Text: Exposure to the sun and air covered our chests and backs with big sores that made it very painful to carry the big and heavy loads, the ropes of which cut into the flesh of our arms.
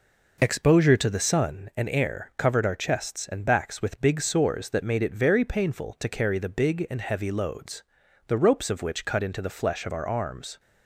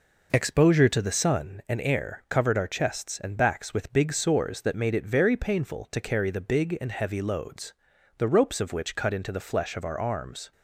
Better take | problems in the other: neither | none

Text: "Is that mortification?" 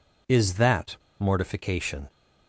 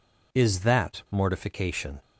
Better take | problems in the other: second | pauses between "that" and "mortification"; slight; at 0.9 s; 0.23 s long

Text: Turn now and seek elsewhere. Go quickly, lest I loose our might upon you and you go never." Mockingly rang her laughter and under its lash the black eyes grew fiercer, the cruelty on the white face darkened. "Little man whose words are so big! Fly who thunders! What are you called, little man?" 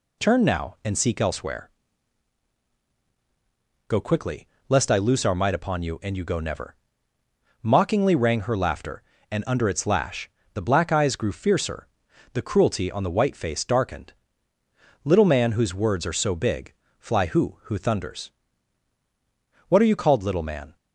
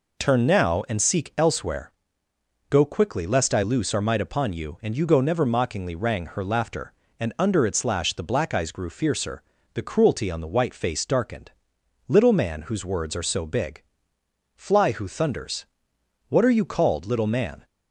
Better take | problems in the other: second | pauses between "lash" and "the"; slight; at 10.2 s; 0.26 s long // says "who" twice; at 17.6 s

